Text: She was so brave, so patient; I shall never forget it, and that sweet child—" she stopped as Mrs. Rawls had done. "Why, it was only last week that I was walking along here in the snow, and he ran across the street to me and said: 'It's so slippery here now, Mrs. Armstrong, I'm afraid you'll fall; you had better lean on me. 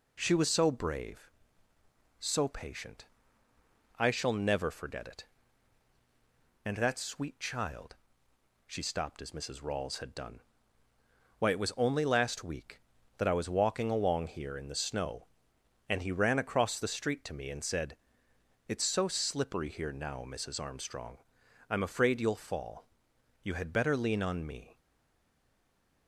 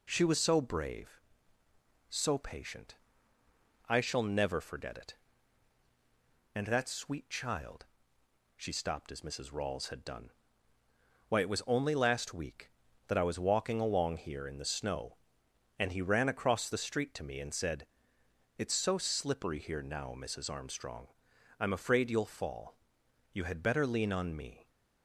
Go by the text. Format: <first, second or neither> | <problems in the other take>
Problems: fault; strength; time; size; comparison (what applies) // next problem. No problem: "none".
second | stays silent after the last word; noticeable; from 24.7 s on; 1.3 s long